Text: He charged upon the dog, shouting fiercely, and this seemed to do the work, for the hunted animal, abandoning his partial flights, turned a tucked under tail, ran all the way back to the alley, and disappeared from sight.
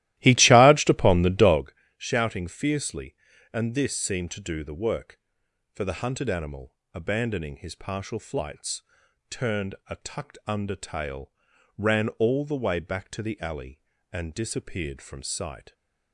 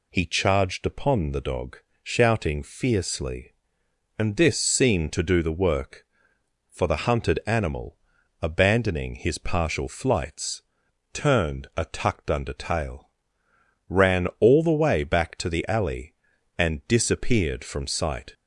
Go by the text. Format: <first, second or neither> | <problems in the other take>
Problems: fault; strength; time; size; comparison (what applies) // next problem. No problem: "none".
second | starts louder than the rest; strong; until 1.7 s; 15.5 dB